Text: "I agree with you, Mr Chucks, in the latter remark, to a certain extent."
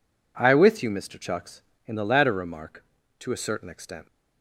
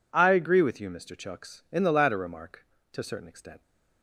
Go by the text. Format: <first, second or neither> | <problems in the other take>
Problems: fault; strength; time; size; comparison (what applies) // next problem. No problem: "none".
second | skips "agree"; at 0.5 s